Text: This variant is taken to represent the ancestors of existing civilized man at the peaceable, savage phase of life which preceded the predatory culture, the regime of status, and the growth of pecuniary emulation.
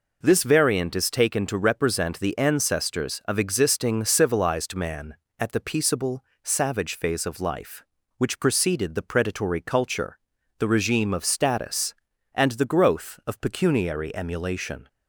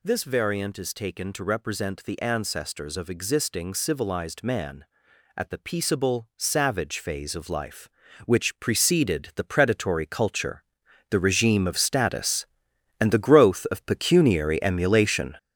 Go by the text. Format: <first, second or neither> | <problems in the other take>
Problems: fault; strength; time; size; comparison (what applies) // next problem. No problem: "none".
first | gets louder; throughout; 7 dB